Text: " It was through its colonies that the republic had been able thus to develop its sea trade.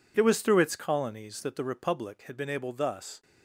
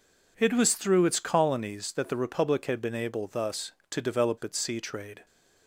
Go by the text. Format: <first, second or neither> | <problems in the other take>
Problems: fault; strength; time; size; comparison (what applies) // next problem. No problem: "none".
second | stops before "to develop its sea trade"; at 3.2 s